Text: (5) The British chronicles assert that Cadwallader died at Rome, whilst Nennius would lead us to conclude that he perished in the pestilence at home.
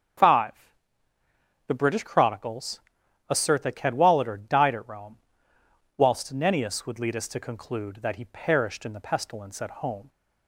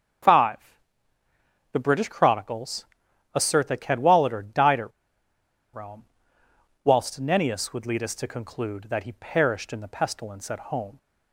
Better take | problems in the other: first | starts louder than the rest; strong; until 2.2 s; 7.5 dB; strong in the first // pauses between "chronicles" and "assert"; noticeable; at 2.8 s; 0.48 s long; noticeable in the first // pauses between "at" and "Rome"; noticeable; at 4.9 s; 0.84 s long

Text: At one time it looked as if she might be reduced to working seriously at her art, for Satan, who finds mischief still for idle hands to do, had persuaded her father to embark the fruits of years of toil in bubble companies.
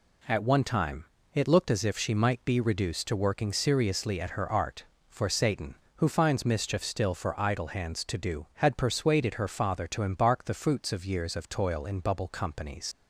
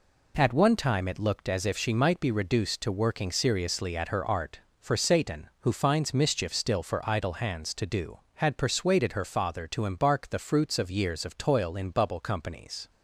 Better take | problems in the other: second | pauses between "time" and "it"; slight; at 1.0 s; 0.30 s long // leaves "companies" unfinished; at 12.9 s; 70 ms

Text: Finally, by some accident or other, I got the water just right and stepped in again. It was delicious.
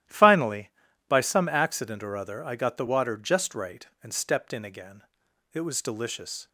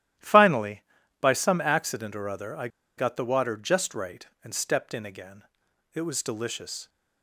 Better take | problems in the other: first | starts louder than the rest; strong; until 1.5 s; 13 dB; strong in the first // pauses between "I" and "got"; slight; at 2.6 s; 0.29 s long

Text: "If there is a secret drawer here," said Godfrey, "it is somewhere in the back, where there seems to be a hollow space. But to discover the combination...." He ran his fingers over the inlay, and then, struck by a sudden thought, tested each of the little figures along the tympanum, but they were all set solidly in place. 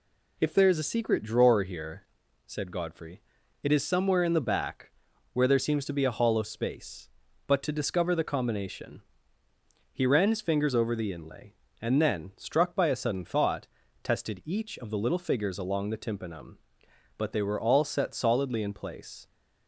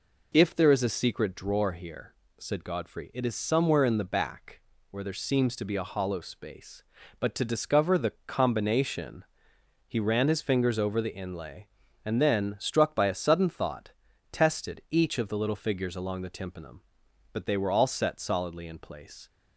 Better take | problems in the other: neither | none

